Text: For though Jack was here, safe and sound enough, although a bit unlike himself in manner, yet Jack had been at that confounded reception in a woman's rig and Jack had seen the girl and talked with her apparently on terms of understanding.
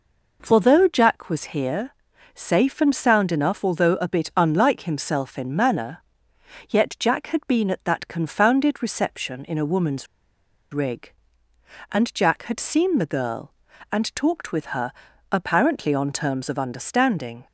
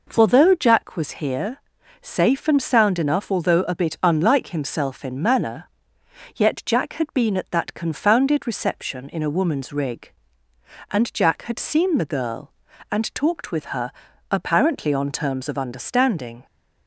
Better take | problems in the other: second | pauses between "woman's" and "rig"; noticeable; at 10.0 s; 0.65 s long // pauses between "her" and "apparently"; at 14.9 s; 0.40 s long; also in the second

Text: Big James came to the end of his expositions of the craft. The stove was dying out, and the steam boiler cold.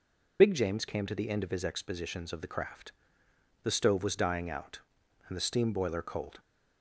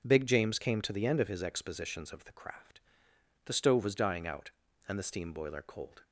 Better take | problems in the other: second | loses the start of "Big"; at 0.3 s; 55 ms

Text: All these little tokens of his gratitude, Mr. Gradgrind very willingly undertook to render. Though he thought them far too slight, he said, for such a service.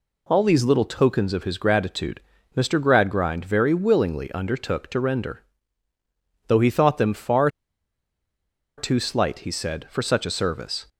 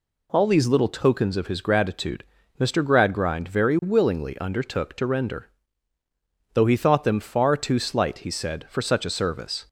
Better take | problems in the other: second | pauses between "far" and "too"; strong; at 7.4 s; 1.2 s long

